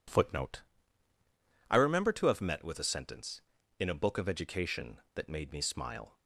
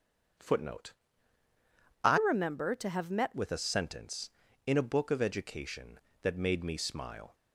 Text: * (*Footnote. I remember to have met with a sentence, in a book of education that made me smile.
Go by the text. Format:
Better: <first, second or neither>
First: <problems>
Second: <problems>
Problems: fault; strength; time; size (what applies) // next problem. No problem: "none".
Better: first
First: none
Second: starts louder than the rest; strong; until 2.4 s; 7 dB // changes voice from "remember" to "met"; from 2.1 to 3.3 s; 1.2 s long